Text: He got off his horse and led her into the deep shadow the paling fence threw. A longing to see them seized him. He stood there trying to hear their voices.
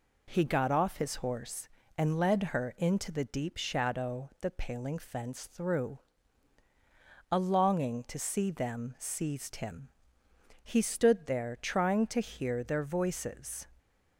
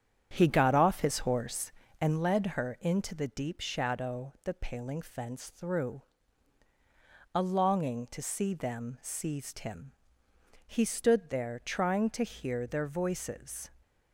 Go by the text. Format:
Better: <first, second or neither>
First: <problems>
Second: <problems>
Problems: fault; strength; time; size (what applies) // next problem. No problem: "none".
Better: first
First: none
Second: starts louder than the rest; strong; until 2.2 s; 8 dB